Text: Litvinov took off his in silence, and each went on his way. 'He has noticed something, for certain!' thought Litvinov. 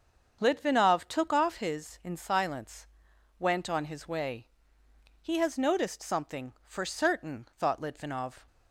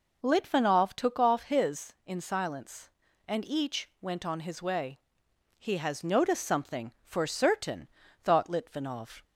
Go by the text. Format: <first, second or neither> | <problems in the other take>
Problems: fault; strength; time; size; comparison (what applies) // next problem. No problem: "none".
second | starts louder than the rest; until 1.4 s; 7 dB // skips "and each"; at 3.1 s